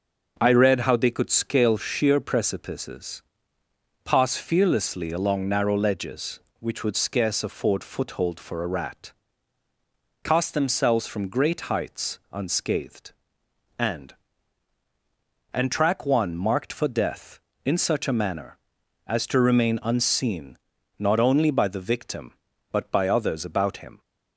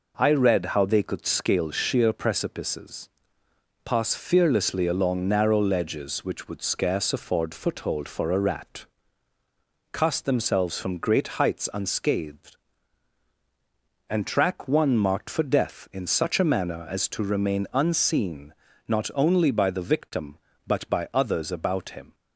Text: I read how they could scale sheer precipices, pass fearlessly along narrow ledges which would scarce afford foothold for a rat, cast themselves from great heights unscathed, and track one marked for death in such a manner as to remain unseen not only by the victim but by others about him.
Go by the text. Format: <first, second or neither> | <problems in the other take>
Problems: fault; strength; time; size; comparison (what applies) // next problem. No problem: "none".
second | says "and" twice; at 15.5 s // pauses between "unseen" and "not"; at 20.5 s; 0.42 s long; slight in the second